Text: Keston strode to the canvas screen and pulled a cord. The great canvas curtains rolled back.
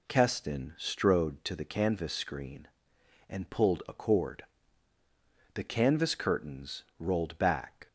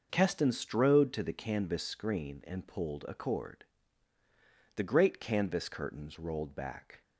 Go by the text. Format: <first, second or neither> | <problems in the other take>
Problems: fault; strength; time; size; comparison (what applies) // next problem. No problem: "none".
second | skips "great"; at 5.6 s // pauses between "curtains" and "rolled"; slight; at 6.8 s; 0.16 s long